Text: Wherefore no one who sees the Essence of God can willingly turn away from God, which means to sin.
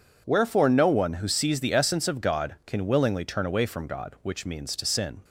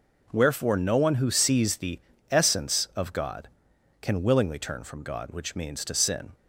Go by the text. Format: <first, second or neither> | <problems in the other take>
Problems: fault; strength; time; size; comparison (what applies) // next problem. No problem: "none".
first | pauses between "the" and "Essence"; slight; at 1.9 s; 0.32 s long // skips "away"; at 4.8 s